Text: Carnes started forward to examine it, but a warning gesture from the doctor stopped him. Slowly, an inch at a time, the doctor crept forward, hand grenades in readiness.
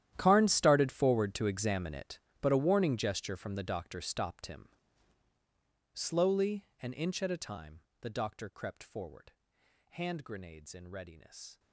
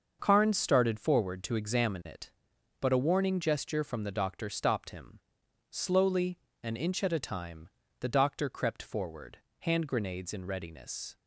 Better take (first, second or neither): second